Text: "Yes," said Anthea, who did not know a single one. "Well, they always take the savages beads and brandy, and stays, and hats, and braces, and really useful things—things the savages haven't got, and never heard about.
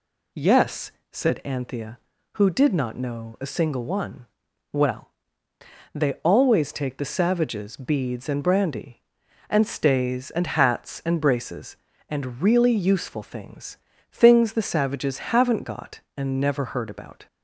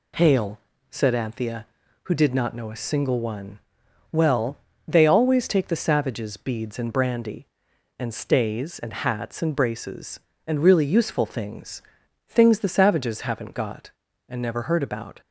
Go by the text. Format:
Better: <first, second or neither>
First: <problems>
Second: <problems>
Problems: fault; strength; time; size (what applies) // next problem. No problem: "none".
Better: first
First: none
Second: says "Hail" for "Yes"; at 0.1 s